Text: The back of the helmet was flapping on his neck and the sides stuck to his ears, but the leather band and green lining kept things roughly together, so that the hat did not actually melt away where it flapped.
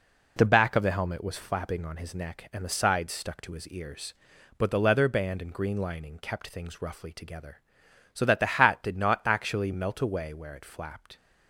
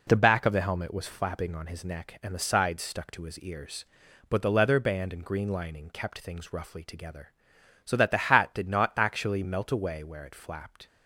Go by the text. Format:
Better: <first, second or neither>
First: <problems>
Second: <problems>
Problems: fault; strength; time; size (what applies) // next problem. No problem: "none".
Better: neither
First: none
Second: none